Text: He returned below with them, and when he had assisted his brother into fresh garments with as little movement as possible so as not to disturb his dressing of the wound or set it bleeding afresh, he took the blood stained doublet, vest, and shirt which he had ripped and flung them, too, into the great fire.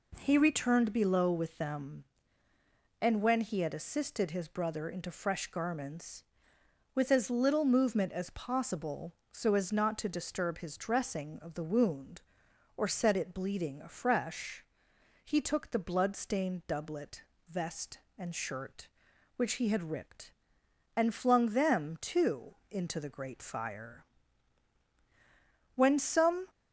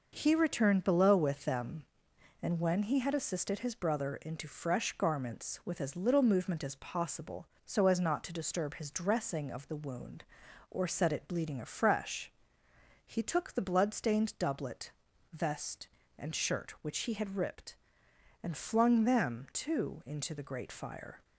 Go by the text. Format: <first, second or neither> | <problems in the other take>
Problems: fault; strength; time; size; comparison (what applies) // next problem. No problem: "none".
second | goes on to say "When some"; noticeable; from 25.7 s on; 0.70 s long